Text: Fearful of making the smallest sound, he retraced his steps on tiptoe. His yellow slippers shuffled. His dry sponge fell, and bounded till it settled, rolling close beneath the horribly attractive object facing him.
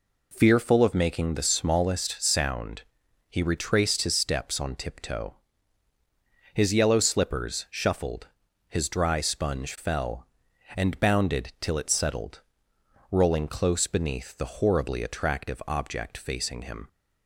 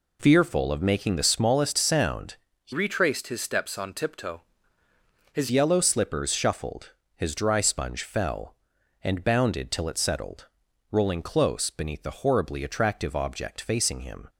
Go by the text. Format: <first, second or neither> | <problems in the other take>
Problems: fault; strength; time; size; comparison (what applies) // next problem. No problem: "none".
first | changes voice from "retraced" to "His"; from 2.7 to 5.4 s; 2.7 s long